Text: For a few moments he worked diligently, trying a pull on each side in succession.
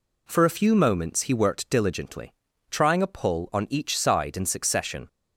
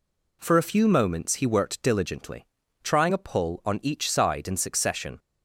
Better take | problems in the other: neither | none

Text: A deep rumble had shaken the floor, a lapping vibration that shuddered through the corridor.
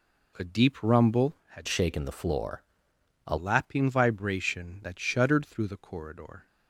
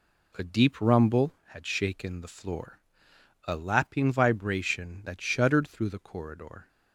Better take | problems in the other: second | changes voice from "shaken" to "a"; from 1.6 to 3.3 s; 1.7 s long

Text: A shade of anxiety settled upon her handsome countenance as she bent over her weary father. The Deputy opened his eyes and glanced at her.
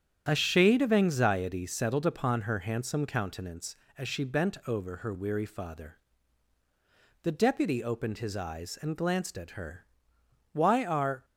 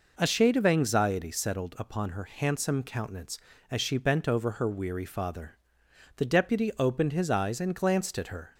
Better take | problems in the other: second | starts louder than the rest; strong; until 1.2 s; 9 dB // goes on to say "Why are"; noticeable; from 10.5 s on; 0.72 s long

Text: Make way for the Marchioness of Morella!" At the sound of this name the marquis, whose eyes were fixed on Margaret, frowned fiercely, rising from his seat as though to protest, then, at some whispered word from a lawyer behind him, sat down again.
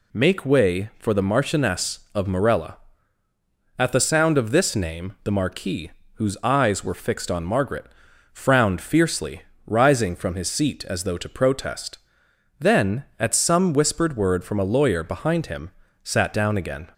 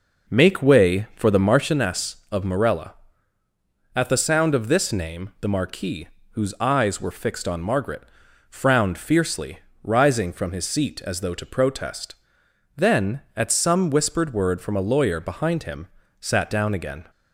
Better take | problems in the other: first | starts louder than the rest; noticeable; until 1.8 s; 5.5 dB

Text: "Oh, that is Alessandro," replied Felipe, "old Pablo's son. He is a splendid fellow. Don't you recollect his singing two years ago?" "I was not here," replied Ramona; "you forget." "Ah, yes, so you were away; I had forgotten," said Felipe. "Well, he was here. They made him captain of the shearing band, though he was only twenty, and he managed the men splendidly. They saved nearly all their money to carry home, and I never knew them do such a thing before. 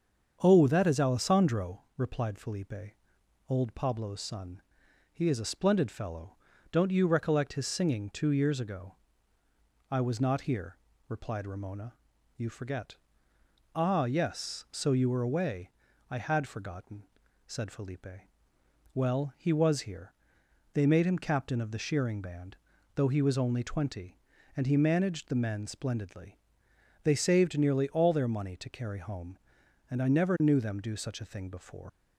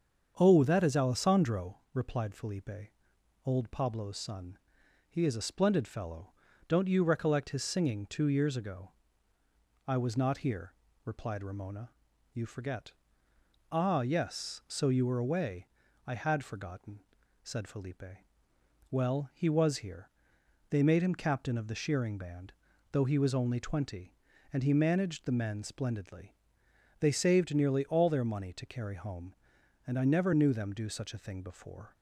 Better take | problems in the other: second | starts louder than the rest; strong; until 1.4 s; 7.5 dB; strong in the second // leaves "before" unfinished; at 31.8 s; 125 ms

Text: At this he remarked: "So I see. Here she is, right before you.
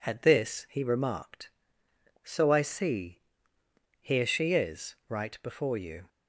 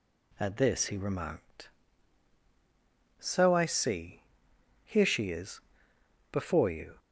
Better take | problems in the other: first | skips "right"; at 5.9 s

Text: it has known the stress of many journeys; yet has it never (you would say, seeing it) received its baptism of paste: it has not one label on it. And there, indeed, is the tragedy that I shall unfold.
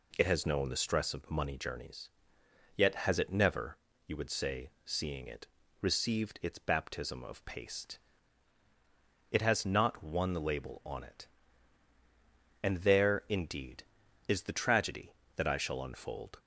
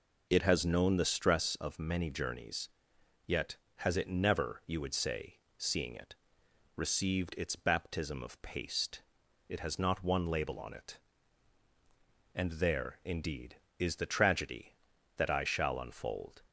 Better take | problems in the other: second | says "money" for "many"; at 1.2 s

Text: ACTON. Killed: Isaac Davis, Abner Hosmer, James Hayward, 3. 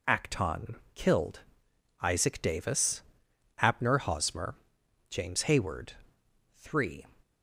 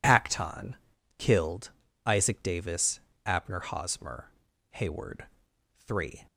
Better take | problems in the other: first | skips "James"; at 4.5 s

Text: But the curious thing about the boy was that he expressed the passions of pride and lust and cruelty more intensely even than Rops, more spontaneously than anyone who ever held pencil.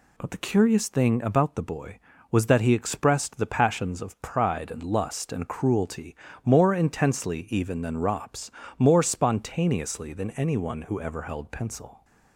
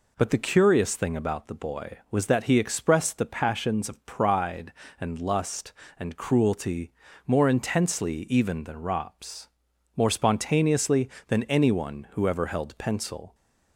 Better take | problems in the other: neither | pauses between "cruelty" and "more"; slight; the same in both

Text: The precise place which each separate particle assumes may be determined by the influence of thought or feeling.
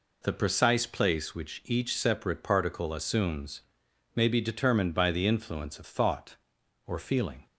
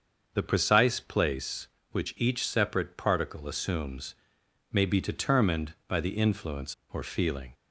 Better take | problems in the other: first | starts louder than the rest; until 1.3 s; 6.5 dB // pauses between "assumes" and "may"; noticeable; at 4.1 s; 0.56 s long; noticeable in the first // skips "of thought"; at 6.8 s

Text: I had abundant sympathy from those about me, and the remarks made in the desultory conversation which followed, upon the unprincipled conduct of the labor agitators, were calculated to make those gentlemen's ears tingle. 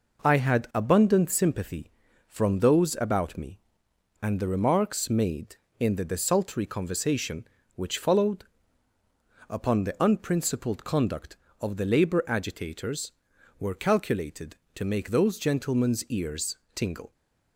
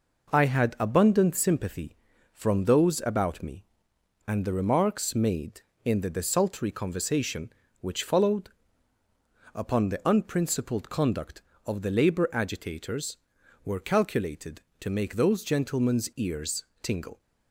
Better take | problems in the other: neither | pauses between "ears" and "tingle"; slight; the same in both

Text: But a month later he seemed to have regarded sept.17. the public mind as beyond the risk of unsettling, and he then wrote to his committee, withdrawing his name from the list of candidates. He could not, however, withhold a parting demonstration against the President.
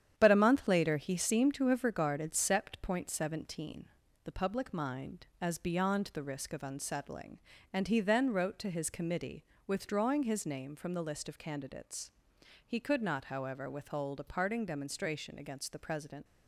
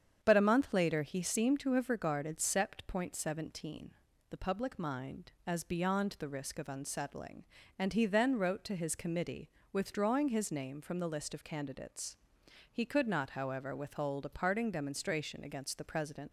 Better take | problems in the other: second | gets quieter; throughout; 6.5 dB // starts louder than the rest; strong; until 1.1 s; 9.5 dB; strong in the second

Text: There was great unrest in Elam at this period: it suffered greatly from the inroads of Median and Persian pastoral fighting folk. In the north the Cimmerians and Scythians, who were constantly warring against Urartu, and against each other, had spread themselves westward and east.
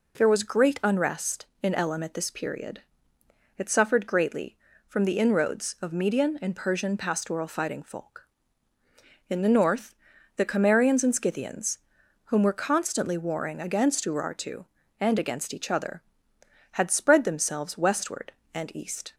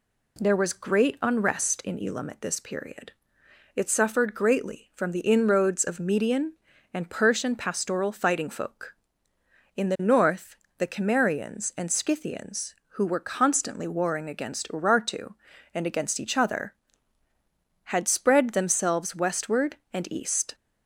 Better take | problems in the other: second | pauses between "north" and "the"; at 9.9 s; 0.40 s long; slight in the second // says "whom" for "who"; at 12.2 s

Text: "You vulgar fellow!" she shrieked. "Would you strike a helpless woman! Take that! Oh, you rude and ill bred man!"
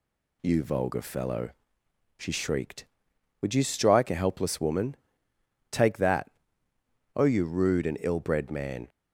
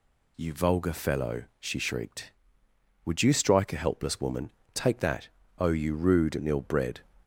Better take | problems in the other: first | stops before "man"; at 7.2 s

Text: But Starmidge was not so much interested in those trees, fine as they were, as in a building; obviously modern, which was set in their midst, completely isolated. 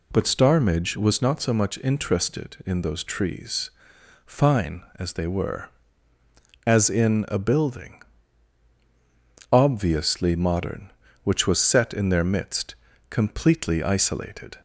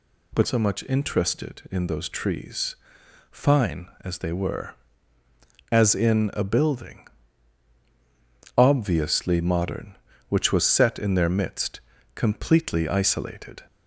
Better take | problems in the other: first | skips "Starmidge was not"; at 0.4 s

